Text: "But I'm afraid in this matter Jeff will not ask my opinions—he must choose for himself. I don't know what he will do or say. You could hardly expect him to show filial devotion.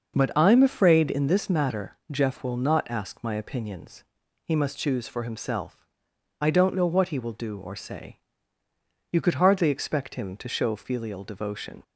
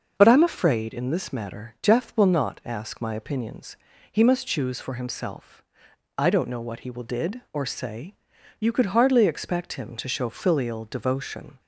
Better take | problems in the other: first | starts louder than the rest; noticeable; until 1.1 s; 6 dB; noticeable in the first // says "did" for "do"; at 7.0 s

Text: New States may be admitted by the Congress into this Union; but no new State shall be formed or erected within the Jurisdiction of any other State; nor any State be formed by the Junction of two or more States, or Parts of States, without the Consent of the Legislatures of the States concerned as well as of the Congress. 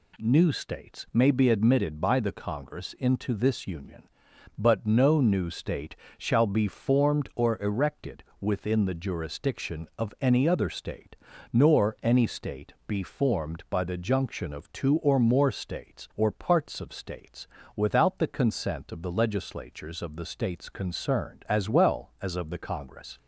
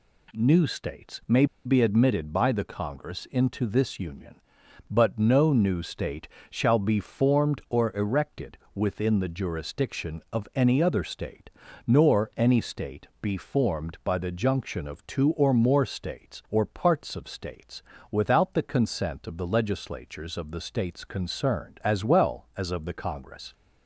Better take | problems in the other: first | pauses between "may" and "be"; slight; at 1.4 s; 0.20 s long // pauses between "State" and "shall"; slight; at 6.2 s; 0.20 s long; slight in the first // pauses between "erected" and "within"; slight; at 8.5 s; 0.16 s long; slight in the first

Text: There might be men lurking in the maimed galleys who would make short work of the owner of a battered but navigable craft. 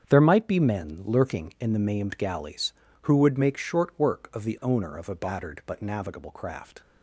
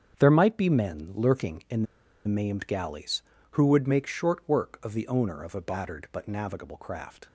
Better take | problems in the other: first | starts louder than the rest; strong; until 1.2 s; 7.5 dB; strong in the first // pauses between "in" and "the"; at 1.8 s; 0.42 s long

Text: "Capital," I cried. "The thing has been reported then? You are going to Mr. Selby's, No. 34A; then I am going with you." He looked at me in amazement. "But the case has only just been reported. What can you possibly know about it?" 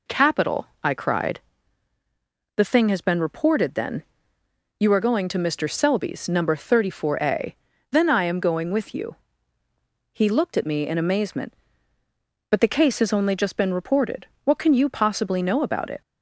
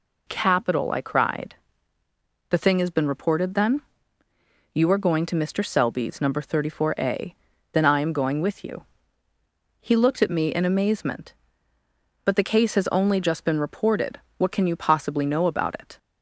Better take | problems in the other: neither | none

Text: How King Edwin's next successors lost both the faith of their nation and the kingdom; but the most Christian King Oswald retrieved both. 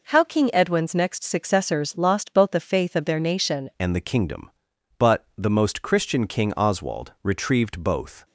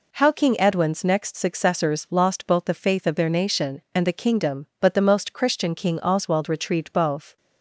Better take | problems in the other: second | changes voice at "and"; from 3.7 s on; 4.5 s long

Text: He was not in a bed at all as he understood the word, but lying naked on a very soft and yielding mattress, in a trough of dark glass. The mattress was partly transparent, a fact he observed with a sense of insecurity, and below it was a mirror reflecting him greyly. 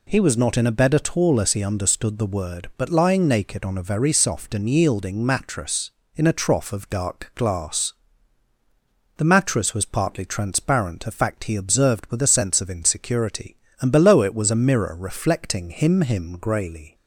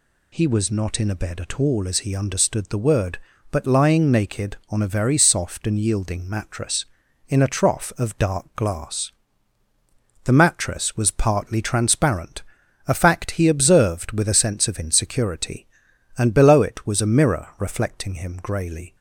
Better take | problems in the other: second | says "him" twice; at 15.9 s

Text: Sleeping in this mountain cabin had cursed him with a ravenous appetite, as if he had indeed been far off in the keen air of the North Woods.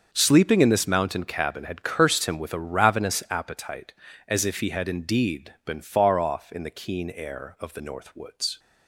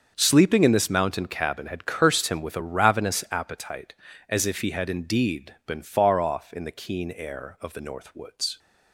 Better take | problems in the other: neither | starts louder than the rest; the same in both

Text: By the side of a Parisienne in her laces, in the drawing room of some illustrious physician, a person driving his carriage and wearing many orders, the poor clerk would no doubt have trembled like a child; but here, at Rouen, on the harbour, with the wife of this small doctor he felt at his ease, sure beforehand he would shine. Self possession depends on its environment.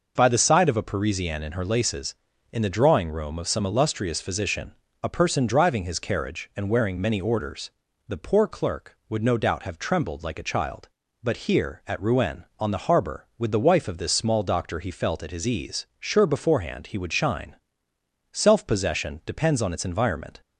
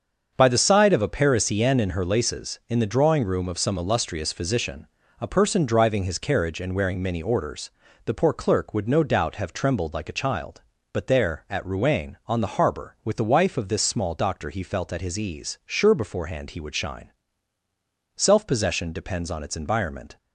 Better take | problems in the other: first | starts louder than the rest; until 1.3 s; 7 dB // says "there" for "here"; at 11.0 s

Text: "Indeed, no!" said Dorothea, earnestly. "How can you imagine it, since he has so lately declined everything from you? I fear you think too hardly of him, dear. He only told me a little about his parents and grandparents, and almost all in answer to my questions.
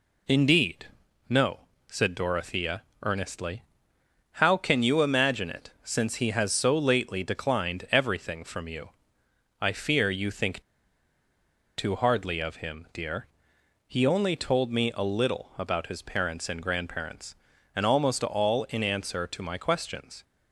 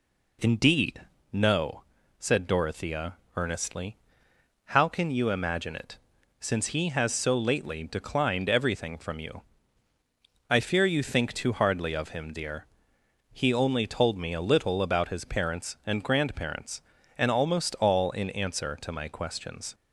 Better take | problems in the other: second | pauses between "think" and "too"; at 10.6 s; 1.1 s long

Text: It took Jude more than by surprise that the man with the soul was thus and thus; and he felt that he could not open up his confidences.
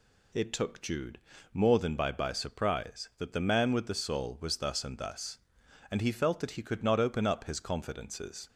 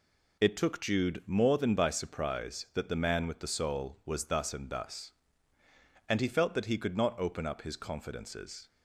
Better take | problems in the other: second | pauses between "Jude" and "more"; slight; at 1.1 s; 0.34 s long // says "by" twice; at 2.0 s

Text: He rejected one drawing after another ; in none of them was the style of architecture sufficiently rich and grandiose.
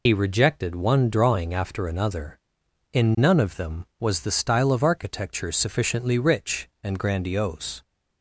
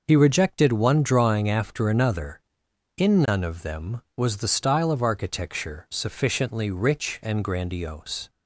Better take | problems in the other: second | loses the start of "He"; at 0.0 s; 60 ms

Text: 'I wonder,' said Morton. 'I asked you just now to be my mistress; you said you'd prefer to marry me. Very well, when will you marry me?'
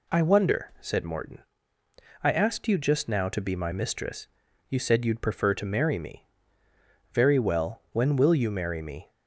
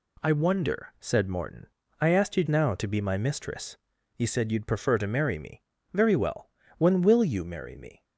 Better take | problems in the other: first | skips "just"; at 2.4 s

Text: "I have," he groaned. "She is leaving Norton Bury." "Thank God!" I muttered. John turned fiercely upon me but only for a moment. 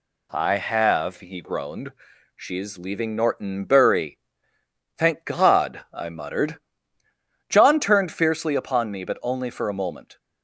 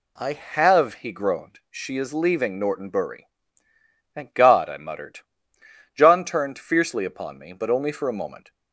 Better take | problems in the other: neither | none

